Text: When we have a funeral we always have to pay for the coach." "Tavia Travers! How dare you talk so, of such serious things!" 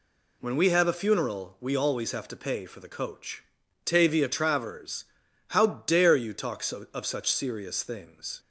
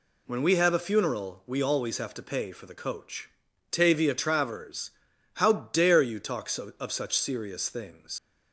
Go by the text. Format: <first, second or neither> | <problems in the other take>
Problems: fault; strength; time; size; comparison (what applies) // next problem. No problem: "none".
first | leaves "things" unfinished; at 8.1 s; 75 ms